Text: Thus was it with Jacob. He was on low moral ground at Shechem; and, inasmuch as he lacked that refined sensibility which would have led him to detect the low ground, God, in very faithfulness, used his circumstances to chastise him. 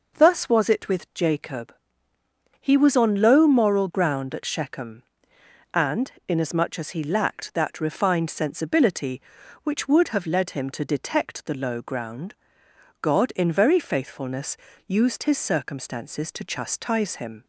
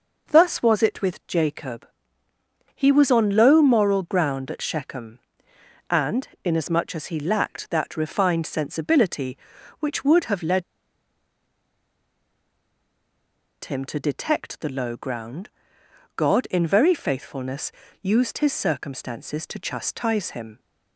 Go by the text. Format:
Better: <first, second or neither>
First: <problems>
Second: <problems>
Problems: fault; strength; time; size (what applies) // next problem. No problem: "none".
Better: first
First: none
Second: pauses between "led" and "him"; strong; at 10.6 s; 3.0 s long